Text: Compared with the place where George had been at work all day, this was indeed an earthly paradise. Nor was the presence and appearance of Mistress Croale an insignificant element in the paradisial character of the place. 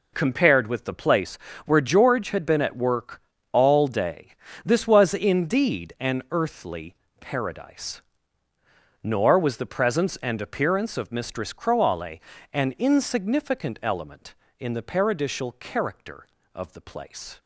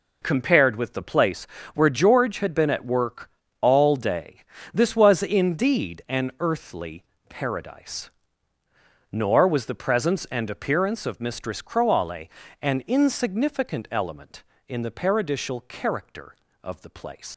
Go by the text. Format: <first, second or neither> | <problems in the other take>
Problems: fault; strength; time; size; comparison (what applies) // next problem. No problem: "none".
first | pauses between "place" and "where"; slight; at 1.4 s; 0.30 s long; slight in the first // pauses between "work" and "all"; slight; at 3.2 s; 0.32 s long; slight in the first // pauses between "earthly" and "paradise"; slight; at 7.0 s; 0.26 s long; slight in the first // pauses between "Croale" and "an"; slight; at 12.2 s; 0.32 s long; slight in the first // leaves "place" unfinished; at 17.3 s; 145 ms